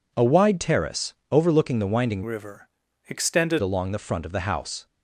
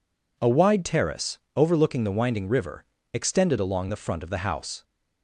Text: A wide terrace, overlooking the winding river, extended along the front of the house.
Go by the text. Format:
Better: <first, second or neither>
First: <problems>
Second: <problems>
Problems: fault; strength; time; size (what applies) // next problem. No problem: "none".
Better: second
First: changes voice from "river" to "extended"; from 2.2 to 3.6 s; 1.4 s long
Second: none